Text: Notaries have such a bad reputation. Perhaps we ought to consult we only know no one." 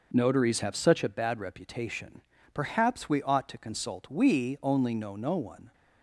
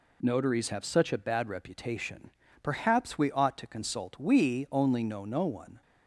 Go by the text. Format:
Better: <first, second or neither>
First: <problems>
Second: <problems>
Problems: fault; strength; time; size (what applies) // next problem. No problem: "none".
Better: second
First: starts louder than the rest; noticeable; until 1.2 s; 6 dB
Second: none